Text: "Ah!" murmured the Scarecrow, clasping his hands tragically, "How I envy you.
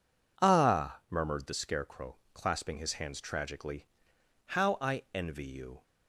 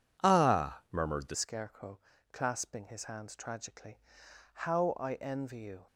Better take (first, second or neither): first